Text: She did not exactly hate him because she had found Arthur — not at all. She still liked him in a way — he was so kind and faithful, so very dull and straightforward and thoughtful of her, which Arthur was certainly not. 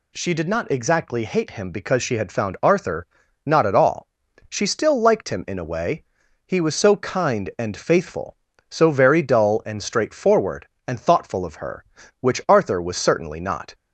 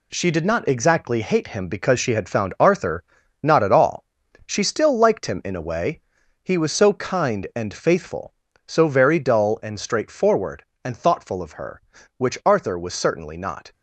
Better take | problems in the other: first | gets quieter; throughout; 6.5 dB

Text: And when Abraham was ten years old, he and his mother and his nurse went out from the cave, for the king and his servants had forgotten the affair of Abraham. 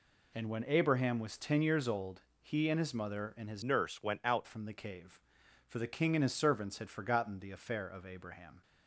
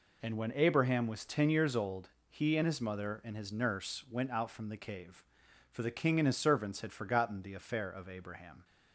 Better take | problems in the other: second | changes voice from "nurse" to "out"; from 3.6 to 4.4 s; 0.8 s long

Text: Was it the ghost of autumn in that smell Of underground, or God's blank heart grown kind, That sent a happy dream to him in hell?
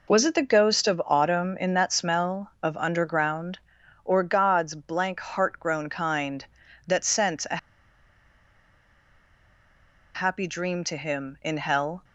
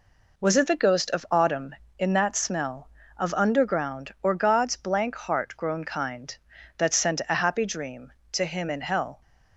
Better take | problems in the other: second | pauses between "a" and "happy"; strong; at 7.5 s; 2.5 s long

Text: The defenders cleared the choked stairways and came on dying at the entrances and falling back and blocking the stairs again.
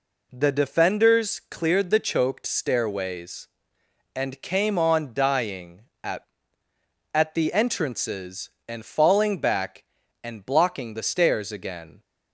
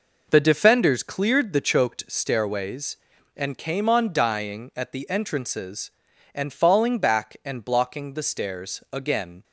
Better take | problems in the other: second | says "at" twice; at 7.1 s

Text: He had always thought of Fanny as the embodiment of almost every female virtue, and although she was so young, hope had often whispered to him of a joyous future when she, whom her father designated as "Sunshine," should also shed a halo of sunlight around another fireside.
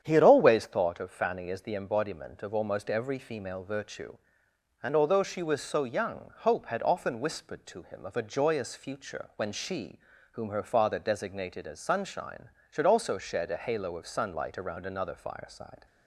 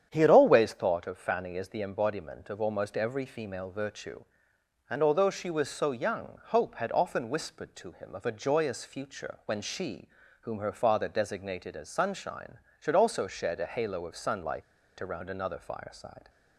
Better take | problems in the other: first | starts louder than the rest; strong; until 1.1 s; 9 dB; strong in the first // pauses between "sunlight" and "around"; at 14.6 s; 0.36 s long

